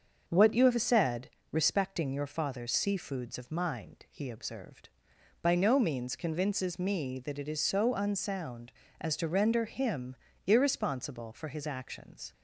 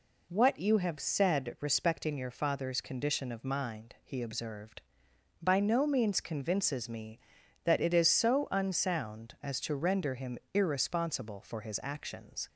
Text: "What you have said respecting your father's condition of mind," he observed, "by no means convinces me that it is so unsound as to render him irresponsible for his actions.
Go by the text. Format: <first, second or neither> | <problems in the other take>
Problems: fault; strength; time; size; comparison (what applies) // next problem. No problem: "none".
second | starts louder than the rest; until 1.2 s; 6.5 dB // pauses between "said" and "respecting"; slight; at 1.3 s; 0.22 s long // says "seafoods" for "condition"; at 2.7 s // pauses between "him" and "irresponsible"; slight; at 10.1 s; 0.28 s long; slight in the second